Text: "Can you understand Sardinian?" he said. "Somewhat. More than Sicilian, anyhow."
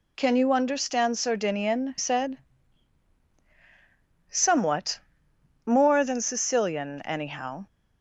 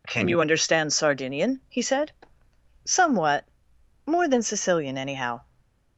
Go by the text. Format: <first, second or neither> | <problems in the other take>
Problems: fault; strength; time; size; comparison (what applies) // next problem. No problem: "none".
second | skips "he"; at 1.9 s